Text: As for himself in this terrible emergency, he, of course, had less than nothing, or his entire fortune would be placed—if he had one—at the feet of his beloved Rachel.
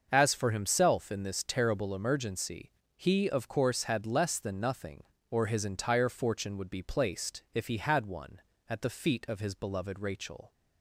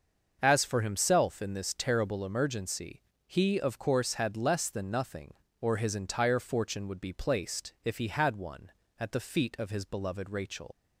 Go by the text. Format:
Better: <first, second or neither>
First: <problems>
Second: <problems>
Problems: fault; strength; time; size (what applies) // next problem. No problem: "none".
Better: first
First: starts louder than the rest; until 1.1 s; 6.5 dB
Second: starts louder than the rest; until 1.4 s; 6.5 dB // leaves "Rachel" unfinished; at 10.7 s; 110 ms